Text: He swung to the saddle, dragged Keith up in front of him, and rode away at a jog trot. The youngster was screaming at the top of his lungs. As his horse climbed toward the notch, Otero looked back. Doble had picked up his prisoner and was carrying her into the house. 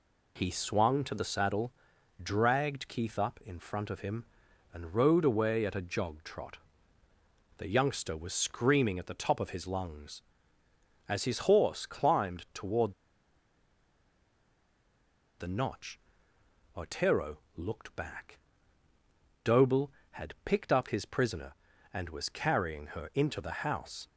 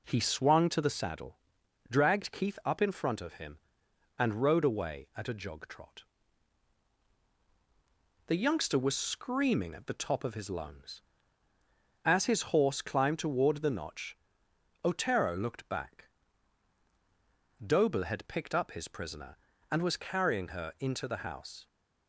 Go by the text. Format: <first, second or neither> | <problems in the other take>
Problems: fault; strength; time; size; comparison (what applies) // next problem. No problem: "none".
second | pauses between "toward" and "the"; strong; at 12.9 s; 2.4 s long // pauses between "Otero" and "looked"; slight; at 17.3 s; 0.18 s long